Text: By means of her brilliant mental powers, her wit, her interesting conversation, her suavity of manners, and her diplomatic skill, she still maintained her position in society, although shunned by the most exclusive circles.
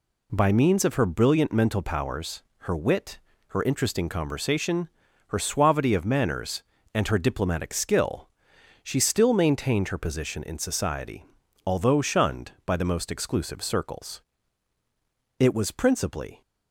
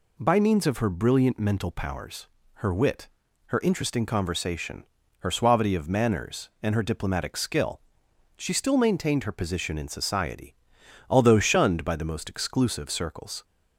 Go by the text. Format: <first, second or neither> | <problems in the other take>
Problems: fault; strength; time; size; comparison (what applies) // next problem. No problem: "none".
second | goes on to say "It was principally"; noticeable; from 15.3 s on; 1.0 s long